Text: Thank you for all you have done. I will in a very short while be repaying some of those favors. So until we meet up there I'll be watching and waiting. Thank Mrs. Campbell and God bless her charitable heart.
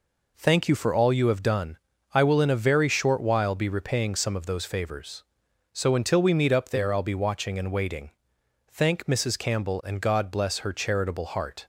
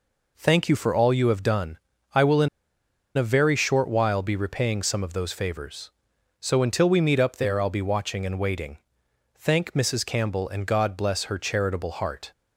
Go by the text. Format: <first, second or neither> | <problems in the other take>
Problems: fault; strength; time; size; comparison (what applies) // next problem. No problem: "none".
first | pauses between "in" and "a"; noticeable; at 2.4 s; 0.69 s long